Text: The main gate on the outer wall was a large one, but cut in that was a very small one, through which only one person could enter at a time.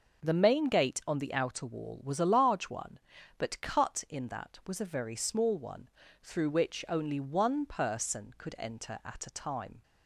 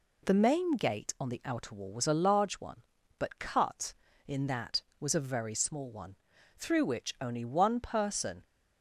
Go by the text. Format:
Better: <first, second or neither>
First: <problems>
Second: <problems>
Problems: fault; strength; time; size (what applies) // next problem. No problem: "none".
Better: first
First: none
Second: stops before "could enter at a time"; at 8.4 s